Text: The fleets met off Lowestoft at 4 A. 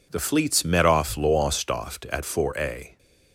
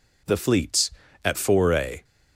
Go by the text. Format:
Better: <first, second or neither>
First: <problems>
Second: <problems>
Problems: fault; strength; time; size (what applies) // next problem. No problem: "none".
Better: first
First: none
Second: skips "met off Lowestoft"; at 1.0 s